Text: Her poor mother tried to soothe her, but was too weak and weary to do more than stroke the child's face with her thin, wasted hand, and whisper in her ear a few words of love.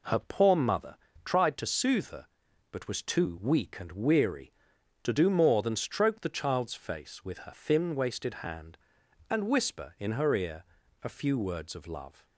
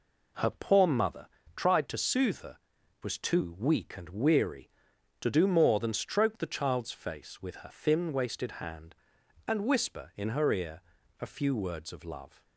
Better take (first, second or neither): first